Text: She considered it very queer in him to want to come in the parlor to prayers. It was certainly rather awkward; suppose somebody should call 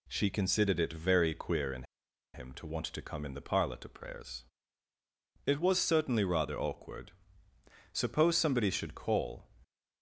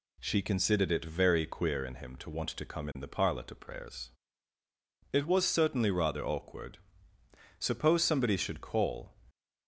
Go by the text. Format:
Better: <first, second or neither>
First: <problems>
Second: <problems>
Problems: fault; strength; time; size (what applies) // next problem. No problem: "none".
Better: second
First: pauses between "in" and "him"; noticeable; at 1.8 s; 0.50 s long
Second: none